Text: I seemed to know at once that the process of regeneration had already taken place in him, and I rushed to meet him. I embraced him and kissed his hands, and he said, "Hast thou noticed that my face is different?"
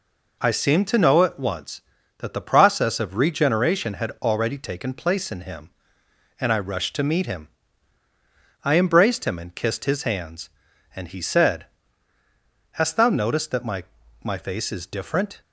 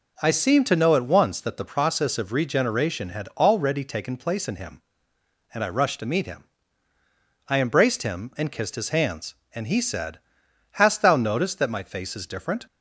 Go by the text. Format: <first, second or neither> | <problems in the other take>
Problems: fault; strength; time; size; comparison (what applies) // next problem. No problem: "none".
second | says "my" twice; at 14.2 s